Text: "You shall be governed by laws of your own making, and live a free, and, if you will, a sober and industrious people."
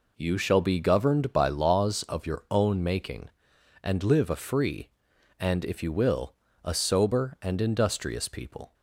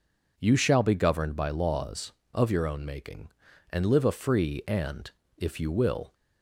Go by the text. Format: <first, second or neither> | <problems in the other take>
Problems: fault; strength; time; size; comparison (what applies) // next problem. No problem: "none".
first | stops before "a sober and industrious people"; at 6.1 s